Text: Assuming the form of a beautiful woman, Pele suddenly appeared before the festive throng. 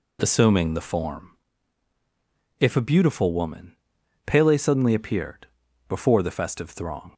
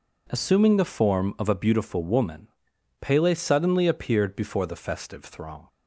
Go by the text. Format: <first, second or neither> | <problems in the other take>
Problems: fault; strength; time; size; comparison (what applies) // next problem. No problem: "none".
second | says "if" for "of"; at 2.5 s // pauses between "appeared" and "before"; at 5.4 s; 0.42 s long